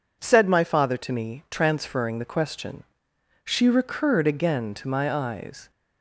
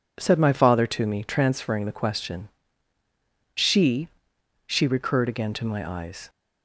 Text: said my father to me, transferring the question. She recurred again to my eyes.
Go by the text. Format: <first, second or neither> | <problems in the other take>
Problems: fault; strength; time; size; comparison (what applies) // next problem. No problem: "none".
first | says "She" twice; at 4.6 s